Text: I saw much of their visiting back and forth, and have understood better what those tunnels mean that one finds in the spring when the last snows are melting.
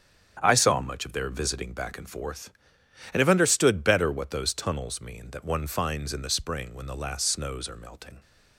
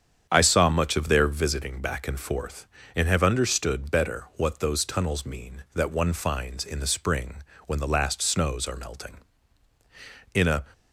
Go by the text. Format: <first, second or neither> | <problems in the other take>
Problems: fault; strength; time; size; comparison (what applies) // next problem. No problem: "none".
first | starts louder than the rest; strong; until 1.3 s; 8 dB; strong in the first // pauses between "spring" and "when"; slight; at 7.3 s; 0.28 s long // goes on to say "In a"; slight; from 10.3 s on; 0.30 s long